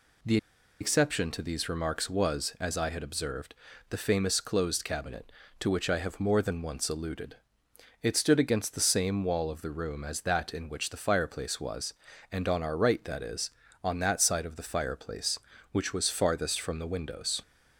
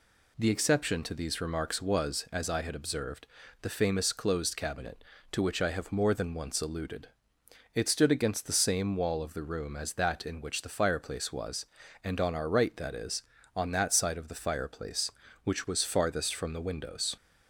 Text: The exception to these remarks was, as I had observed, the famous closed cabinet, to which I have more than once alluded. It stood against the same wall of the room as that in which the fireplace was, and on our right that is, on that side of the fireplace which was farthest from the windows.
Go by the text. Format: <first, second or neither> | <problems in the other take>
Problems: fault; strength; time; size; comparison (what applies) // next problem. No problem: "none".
second | pauses between "The" and "exception"; at 0.3 s; 0.43 s long